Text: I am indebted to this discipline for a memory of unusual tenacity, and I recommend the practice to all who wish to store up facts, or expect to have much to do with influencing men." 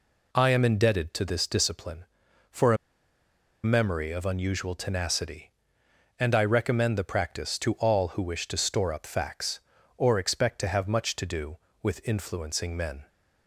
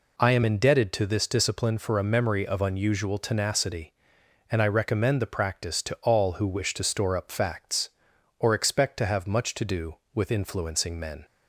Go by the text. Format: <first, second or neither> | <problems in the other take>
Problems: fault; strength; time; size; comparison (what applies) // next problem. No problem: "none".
second | pauses between "a" and "memory"; noticeable; at 2.7 s; 0.87 s long